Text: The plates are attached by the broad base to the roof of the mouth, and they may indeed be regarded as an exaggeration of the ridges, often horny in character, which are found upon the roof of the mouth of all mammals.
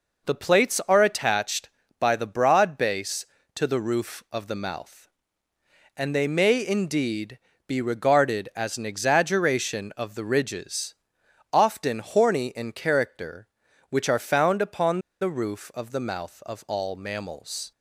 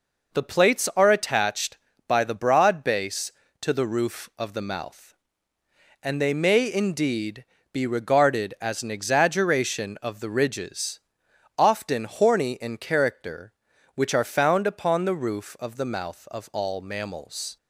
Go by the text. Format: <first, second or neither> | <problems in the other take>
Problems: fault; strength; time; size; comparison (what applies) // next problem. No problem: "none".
second | pauses between "indeed" and "be"; slight; at 7.3 s; 0.28 s long; slight in the second // pauses between "upon" and "the"; slight; at 15.0 s; 0.20 s long